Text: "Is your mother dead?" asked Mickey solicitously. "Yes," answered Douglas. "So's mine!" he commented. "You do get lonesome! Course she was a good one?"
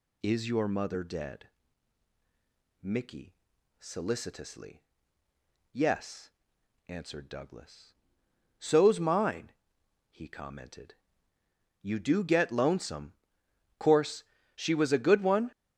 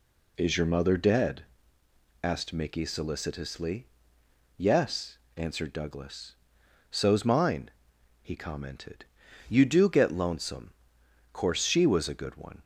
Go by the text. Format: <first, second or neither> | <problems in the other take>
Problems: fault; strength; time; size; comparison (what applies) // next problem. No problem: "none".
second | skips "asked"; at 2.1 s // pauses between "Mickey" and "solicitously"; noticeable; at 3.3 s; 0.46 s long // pauses between "Course" and "she"; slight; at 14.2 s; 0.32 s long